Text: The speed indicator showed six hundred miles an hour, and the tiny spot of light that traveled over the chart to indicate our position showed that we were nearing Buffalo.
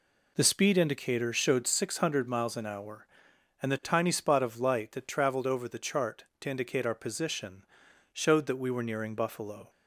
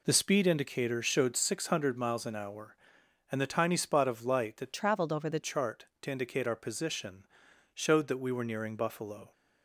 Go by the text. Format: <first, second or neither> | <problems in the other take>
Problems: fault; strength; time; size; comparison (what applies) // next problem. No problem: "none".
first | changes voice from "traveled" to "the"; from 4.7 to 5.4 s; 0.7 s long // pauses between "position" and "showed"; noticeable; at 7.2 s; 0.48 s long; noticeable in the first